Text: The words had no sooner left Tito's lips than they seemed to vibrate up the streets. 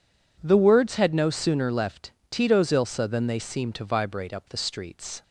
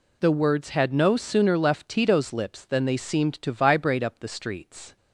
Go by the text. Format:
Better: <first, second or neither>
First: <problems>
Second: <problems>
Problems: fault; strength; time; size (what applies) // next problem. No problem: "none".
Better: second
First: pauses between "left" and "Tito's"; slight; at 2.1 s; 0.18 s long // says "ilsa" for "lips"; at 2.7 s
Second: none